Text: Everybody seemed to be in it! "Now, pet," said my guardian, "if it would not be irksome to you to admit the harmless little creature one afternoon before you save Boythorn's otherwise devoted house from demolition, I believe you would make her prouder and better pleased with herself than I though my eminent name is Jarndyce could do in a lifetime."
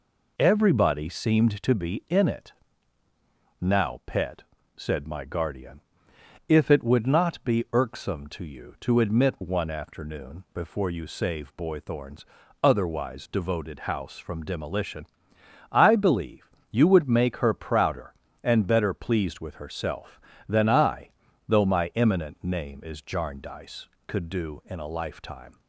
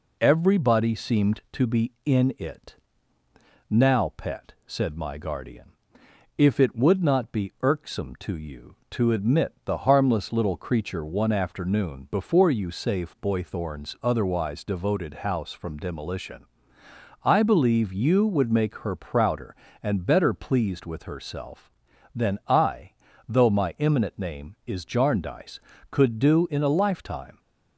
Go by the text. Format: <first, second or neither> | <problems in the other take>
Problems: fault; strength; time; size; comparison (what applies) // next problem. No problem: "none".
second | skips "the harmless little creature"; at 9.4 s // pauses between "Boythorn's" and "otherwise"; slight; at 12.2 s; 0.36 s long // pauses between "believe" and "you"; slight; at 16.5 s; 0.22 s long // pauses between "I" and "though"; slight; at 21.1 s; 0.36 s long; slight in the second